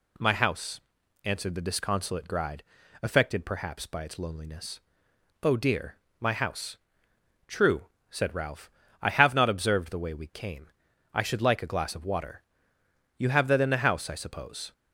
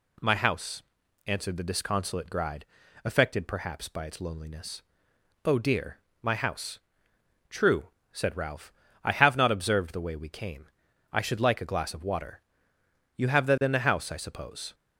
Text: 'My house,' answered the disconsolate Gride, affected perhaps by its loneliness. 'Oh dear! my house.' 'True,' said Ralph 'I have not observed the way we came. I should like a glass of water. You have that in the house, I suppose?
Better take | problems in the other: neither | pauses between "Ralph" and "I"; slight; the same in both

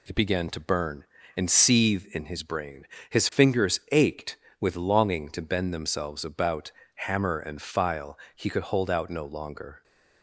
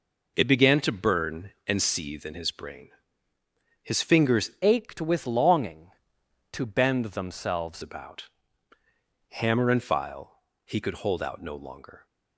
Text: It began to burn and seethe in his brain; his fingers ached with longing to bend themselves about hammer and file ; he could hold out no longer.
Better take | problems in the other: first | changes voice from "ached" to "themselves"; from 4.6 to 7.8 s; 3.2 s long // pauses between "about" and "hammer"; noticeable; at 8.2 s; 0.98 s long; slight in the first

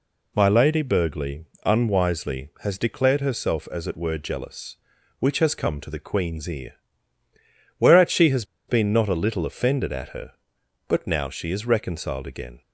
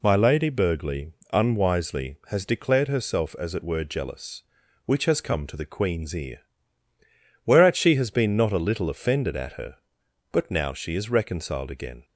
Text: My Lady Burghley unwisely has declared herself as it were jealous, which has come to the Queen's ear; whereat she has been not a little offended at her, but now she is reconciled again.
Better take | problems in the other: second | pauses between "Burghley" and "unwisely"; slight; at 1.4 s; 0.18 s long; slight in the second // pauses between "has" and "been"; slight; at 8.4 s; 0.24 s long

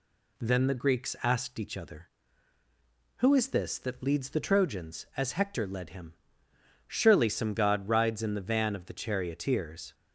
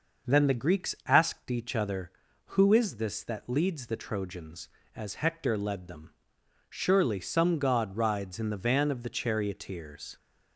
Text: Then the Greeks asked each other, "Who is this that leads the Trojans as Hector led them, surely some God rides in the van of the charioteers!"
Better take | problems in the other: second | says "him" for "them"; at 5.8 s

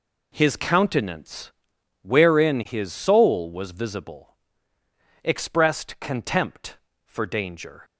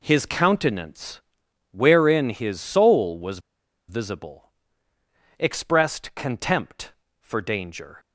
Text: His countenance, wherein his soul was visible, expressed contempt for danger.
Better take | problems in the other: first | pauses between "was" and "visible"; noticeable; at 3.3 s; 0.50 s long

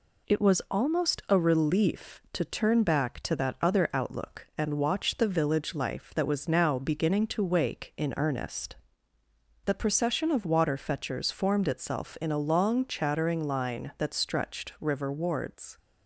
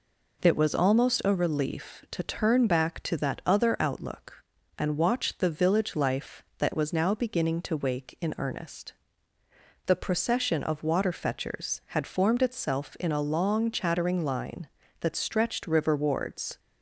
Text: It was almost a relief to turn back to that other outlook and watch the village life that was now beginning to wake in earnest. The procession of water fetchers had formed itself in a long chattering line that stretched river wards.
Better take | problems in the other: second | skips "had"; at 11.3 s

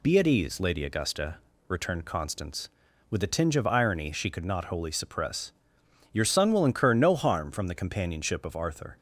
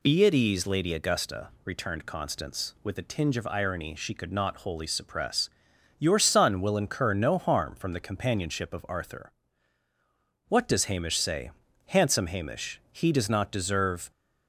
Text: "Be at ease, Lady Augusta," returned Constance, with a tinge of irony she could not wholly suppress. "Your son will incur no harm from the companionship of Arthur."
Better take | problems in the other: first | goes on to say "What does Hamish say handsome Hamish He does not deserve"; strong; from 10.4 s on; 3.6 s long

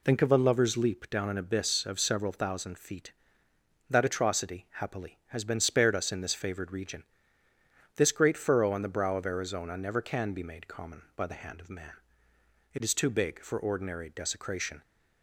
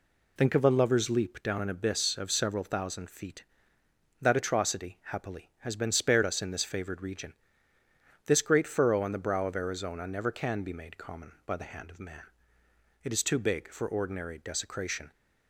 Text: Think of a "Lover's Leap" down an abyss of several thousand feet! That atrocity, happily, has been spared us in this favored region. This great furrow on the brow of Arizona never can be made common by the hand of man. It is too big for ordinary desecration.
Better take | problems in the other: neither | none

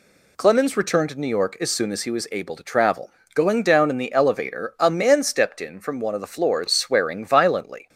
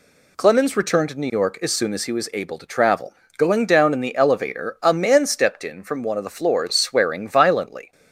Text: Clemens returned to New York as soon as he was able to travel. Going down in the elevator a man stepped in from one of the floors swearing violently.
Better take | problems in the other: neither | none

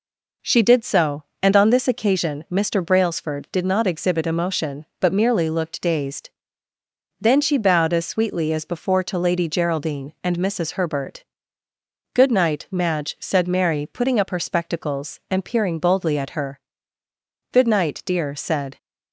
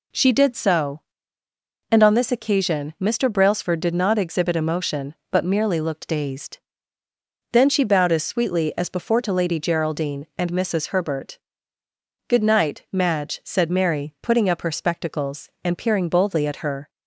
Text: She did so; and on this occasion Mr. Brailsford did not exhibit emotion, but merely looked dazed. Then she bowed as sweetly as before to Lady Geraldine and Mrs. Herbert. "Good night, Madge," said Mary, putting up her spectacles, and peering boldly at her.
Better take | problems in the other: second | goes on to say "Good night dear said"; noticeable; from 17.5 s on; 1.2 s long

